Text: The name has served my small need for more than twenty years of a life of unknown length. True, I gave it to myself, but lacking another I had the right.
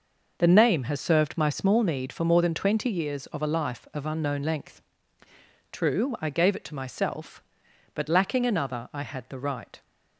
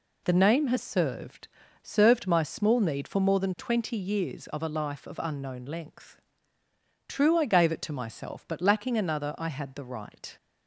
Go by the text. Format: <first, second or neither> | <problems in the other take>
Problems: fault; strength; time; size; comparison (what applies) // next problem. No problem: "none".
first | says "served" twice; at 1.8 s